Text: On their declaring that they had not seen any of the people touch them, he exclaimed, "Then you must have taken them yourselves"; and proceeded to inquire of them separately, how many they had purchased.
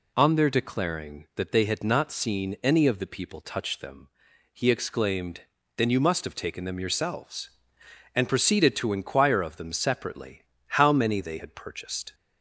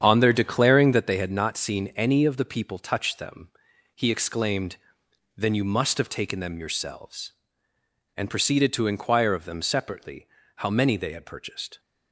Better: first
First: none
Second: starts louder than the rest; strong; until 1.1 s; 8 dB

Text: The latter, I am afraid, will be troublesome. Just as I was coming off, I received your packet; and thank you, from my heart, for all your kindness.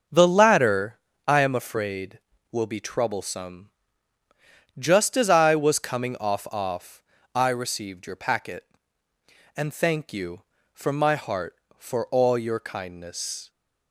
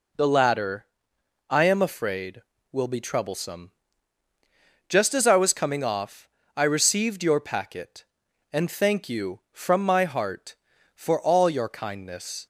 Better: second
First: starts louder than the rest; noticeable; until 1.3 s; 6 dB // says "off" twice; at 6.4 s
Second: none

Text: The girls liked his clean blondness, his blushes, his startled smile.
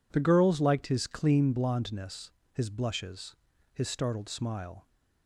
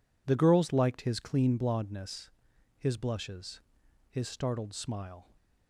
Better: neither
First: none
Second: none

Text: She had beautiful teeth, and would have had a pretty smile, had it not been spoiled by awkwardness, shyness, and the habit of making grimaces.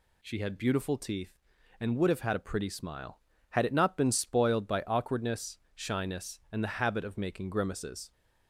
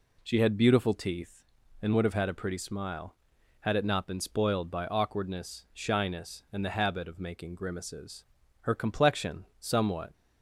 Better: first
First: none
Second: goes on to say "Her complexion somewhat"; from 8.6 s on; 1.5 s long

